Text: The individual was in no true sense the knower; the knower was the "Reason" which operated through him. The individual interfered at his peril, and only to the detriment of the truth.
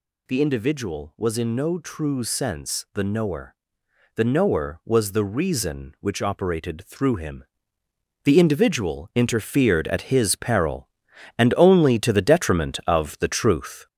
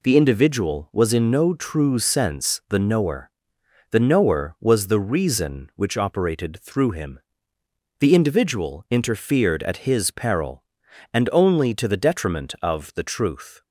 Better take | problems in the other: second | gets louder; noticeable; throughout; 5 dB

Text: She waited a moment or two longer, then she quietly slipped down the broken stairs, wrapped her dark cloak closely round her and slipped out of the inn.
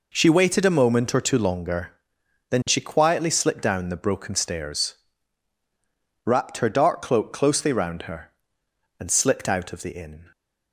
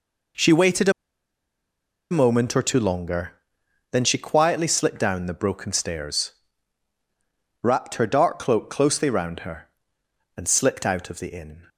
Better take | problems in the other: first | pauses between "waited" and "a"; at 0.8 s; 1.2 s long

